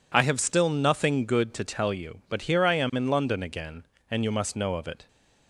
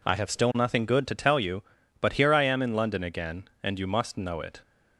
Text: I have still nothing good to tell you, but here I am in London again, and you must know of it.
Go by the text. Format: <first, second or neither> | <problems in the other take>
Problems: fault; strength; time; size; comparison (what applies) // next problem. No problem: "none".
first | skips "of"; at 4.3 s